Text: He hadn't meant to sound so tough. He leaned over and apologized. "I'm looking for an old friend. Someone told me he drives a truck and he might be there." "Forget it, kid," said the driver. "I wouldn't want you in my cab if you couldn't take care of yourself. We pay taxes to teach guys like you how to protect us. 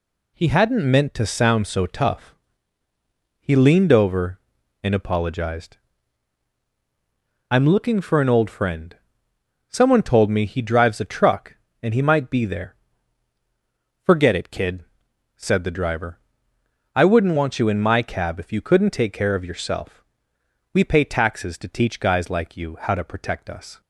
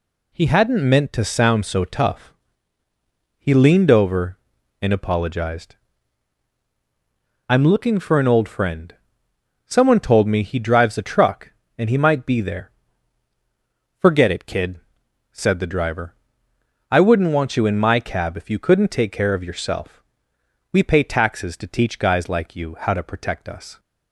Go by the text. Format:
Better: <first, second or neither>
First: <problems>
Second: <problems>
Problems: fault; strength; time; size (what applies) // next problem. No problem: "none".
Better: neither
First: none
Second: none